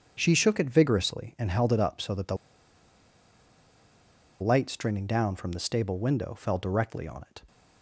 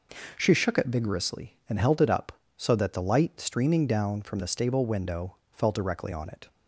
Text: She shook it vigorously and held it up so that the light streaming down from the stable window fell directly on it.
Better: second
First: starts louder than the rest; strong; until 1.1 s; 7.5 dB // pauses between "the" and "light"; strong; at 2.3 s; 2.0 s long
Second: none

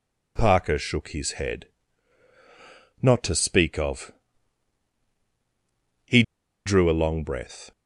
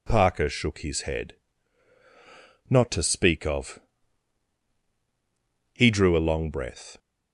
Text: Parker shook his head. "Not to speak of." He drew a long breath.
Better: second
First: pauses between "He" and "drew"; at 6.2 s; 0.43 s long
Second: none

